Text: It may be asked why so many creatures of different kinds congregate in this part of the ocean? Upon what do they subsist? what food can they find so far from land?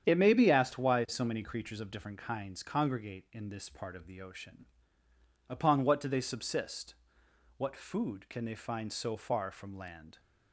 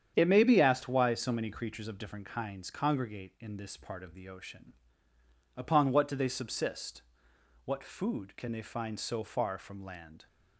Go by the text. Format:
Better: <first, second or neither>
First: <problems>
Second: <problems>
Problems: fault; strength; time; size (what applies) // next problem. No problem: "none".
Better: neither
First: starts louder than the rest; strong; until 1.1 s; 8.5 dB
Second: starts louder than the rest; strong; until 1.1 s; 8.5 dB